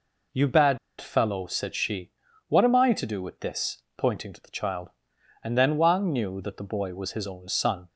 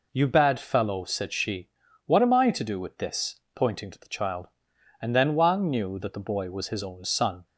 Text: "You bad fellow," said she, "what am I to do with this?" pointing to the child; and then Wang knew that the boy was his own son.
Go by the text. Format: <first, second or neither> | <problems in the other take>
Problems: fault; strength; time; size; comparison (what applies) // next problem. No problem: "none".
second | pauses between "bad" and "fellow"; slight; at 0.7 s; 0.21 s long